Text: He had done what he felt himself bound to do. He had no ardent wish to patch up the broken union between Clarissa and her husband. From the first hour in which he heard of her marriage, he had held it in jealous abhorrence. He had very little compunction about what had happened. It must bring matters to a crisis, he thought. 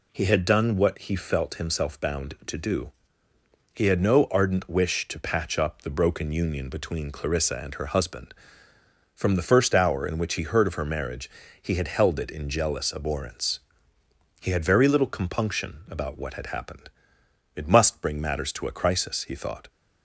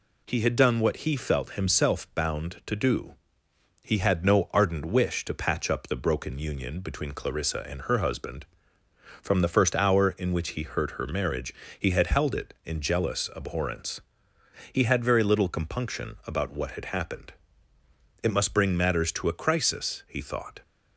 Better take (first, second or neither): first